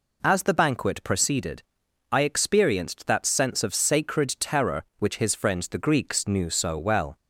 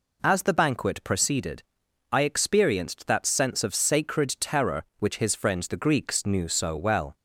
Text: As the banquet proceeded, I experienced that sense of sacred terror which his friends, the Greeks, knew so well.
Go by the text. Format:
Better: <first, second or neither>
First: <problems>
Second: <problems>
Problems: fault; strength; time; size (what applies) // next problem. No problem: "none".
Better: neither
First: none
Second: none